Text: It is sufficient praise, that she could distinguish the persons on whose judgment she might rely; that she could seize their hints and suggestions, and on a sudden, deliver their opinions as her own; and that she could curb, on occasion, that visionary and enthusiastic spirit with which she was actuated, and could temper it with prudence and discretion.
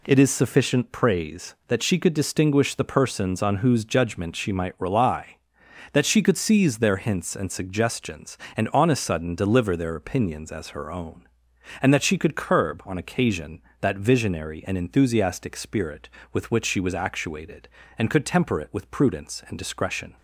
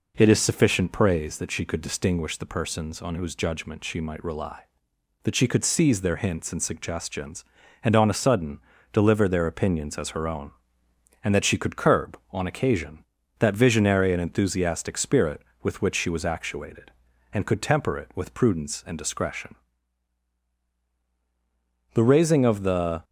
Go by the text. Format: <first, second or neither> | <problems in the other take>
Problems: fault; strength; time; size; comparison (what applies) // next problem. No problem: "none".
first | goes on to say "The raising of the"; noticeable; from 21.9 s on; 1.1 s long